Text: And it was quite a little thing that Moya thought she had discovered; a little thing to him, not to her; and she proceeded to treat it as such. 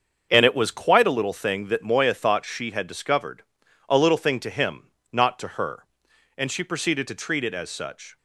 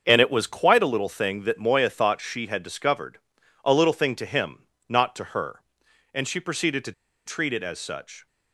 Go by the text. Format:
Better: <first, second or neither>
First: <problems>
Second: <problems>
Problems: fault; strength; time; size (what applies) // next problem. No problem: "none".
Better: first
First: starts louder than the rest; until 1.3 s; 7 dB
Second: starts louder than the rest; until 1.0 s; 7 dB // pauses between "to" and "treat"; slight; at 6.9 s; 0.33 s long